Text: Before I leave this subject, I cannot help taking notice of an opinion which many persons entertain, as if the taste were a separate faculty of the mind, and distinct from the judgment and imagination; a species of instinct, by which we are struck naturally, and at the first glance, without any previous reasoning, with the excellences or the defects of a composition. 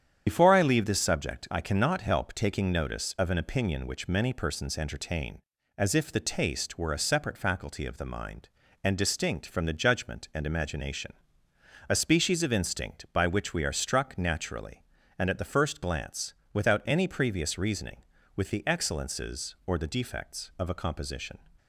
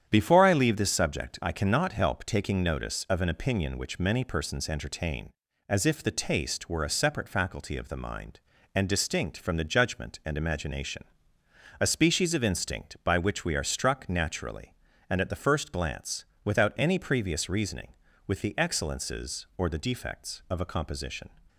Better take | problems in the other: second | loses the start of "Before"; at 0.2 s; 80 ms // starts louder than the rest; strong; until 1.2 s; 8.5 dB; strong in the second

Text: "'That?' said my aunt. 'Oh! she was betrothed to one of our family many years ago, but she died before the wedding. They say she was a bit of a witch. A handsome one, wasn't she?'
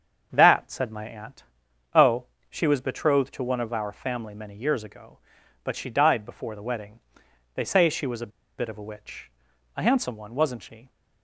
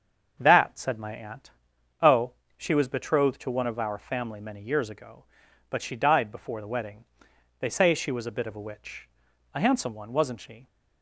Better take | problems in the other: second | starts louder than the rest; until 1.3 s; 7 dB; also in the second // pauses between "a" and "bit"; slight; at 8.2 s; 0.30 s long

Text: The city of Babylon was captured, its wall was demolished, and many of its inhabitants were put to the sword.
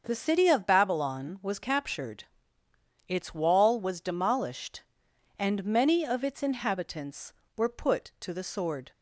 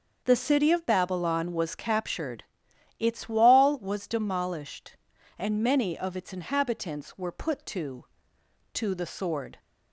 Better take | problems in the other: first | starts louder than the rest; until 1.2 s; 6.5 dB; also in the first // says "to" twice; at 8.7 s

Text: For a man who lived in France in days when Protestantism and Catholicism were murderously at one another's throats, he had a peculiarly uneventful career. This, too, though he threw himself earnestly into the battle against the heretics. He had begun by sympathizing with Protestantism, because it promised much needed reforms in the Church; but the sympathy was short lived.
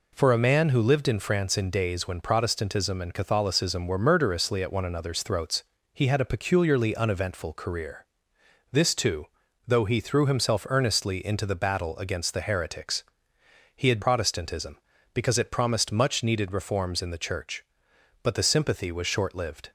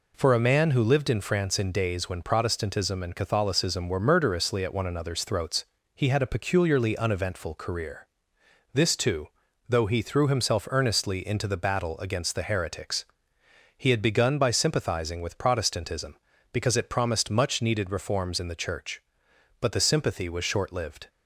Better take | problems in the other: second | skips "begun by sympathizing with"; at 14.0 s

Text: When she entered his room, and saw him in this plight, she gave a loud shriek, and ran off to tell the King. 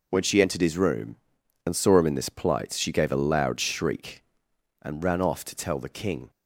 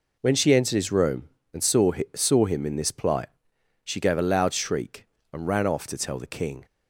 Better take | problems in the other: first | says "saw" twice; at 2.1 s

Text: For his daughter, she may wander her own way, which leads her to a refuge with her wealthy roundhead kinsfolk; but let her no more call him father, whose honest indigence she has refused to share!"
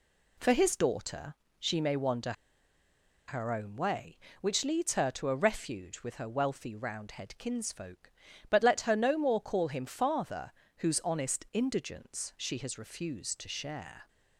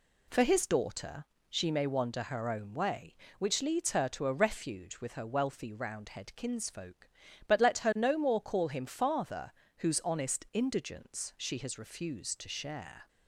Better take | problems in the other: second | pauses between "wander" and "her"; noticeable; at 2.3 s; 0.95 s long

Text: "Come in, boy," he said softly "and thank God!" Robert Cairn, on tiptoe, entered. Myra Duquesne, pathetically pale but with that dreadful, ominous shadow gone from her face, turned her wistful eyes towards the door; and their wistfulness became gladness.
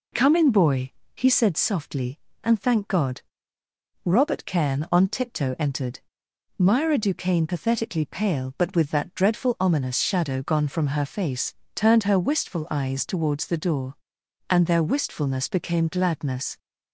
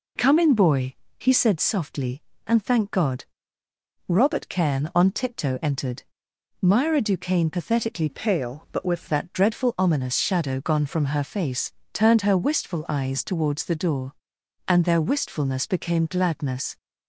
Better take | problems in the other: first | changes voice from "pale" to "with"; from 8.0 to 9.0 s; 1.0 s long

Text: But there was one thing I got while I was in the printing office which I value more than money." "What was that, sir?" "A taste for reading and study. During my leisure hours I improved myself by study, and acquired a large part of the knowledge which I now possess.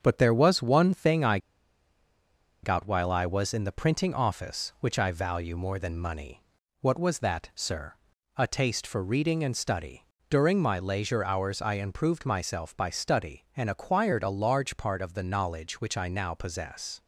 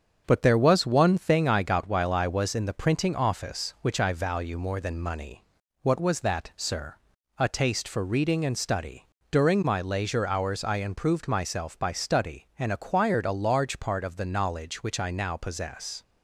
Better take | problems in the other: second | starts louder than the rest; until 1.0 s; 7 dB; also in the second // pauses between "I" and "got"; strong; at 1.3 s; 1.2 s long

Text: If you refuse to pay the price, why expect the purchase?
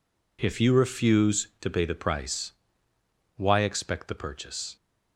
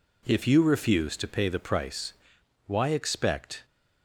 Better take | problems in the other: first | stops before "the purchase"; at 3.6 s

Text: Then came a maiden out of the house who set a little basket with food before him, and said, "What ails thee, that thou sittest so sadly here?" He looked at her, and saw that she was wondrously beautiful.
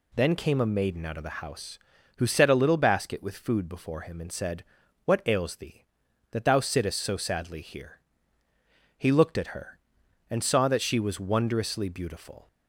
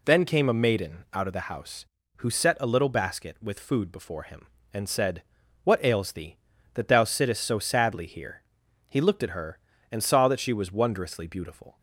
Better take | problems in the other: neither | none

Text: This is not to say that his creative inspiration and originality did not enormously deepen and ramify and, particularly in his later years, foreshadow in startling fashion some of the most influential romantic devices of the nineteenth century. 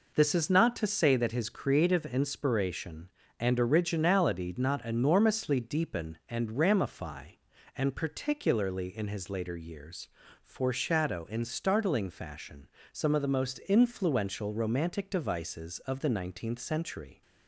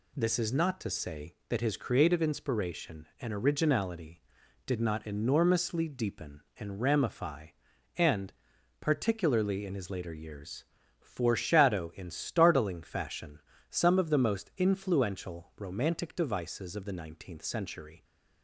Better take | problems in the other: second | skips "did"; at 4.5 s // pauses between "fashion" and "some"; slight; at 12.6 s; 0.24 s long; slight in the second

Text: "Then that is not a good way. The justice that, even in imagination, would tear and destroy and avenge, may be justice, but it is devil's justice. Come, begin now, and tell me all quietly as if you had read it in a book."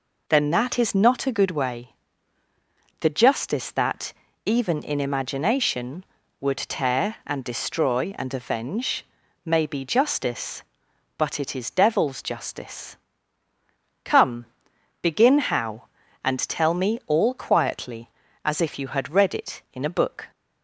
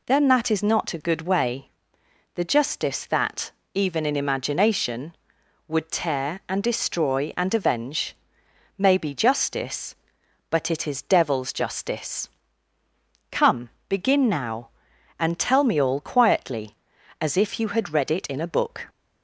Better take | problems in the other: second | says "how" for "now"; at 15.3 s

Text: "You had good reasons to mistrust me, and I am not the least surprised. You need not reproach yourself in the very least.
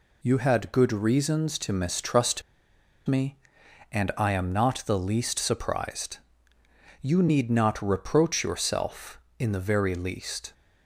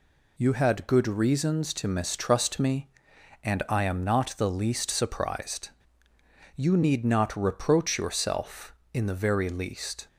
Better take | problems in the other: second | pauses between "mistrust" and "me"; noticeable; at 2.4 s; 0.64 s long

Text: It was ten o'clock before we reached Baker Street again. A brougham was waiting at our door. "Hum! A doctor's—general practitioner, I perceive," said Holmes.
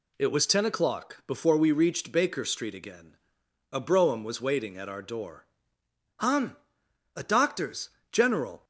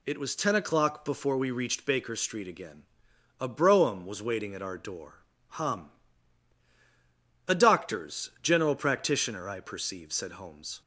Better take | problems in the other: second | stops before "practitioner I perceive said Holmes"; at 8.6 s

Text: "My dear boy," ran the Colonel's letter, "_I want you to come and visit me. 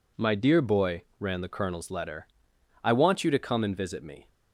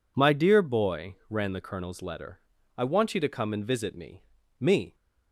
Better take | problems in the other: first | says "me" twice; at 4.6 s

